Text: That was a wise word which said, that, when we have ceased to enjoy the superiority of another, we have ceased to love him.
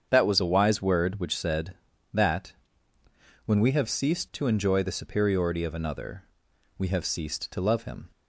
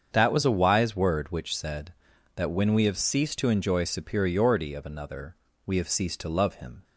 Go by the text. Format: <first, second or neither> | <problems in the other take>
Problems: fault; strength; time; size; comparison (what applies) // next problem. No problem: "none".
first | starts louder than the rest; strong; until 1.1 s; 7 dB; strong in the first // skips "the"; at 3.8 s